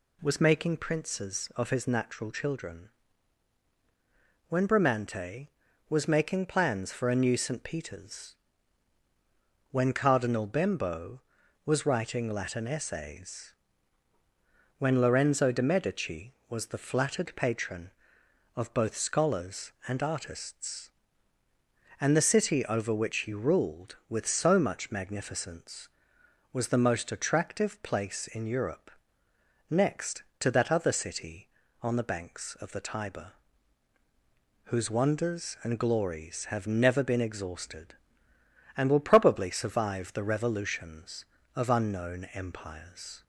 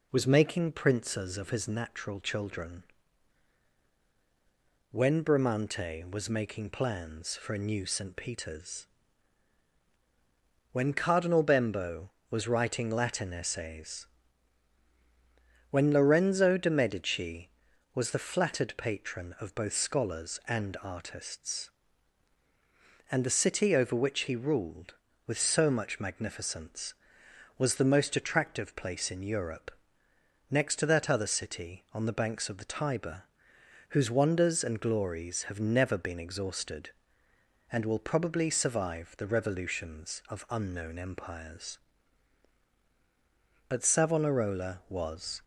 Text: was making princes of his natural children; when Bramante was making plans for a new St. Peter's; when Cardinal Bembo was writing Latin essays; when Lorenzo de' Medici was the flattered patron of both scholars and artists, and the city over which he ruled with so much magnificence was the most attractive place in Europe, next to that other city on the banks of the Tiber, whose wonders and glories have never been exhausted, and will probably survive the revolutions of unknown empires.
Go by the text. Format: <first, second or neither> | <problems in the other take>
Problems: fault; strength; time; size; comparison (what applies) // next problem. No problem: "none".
first | goes on to say "But Savonarola was"; strong; from 43.6 s on; 1.7 s long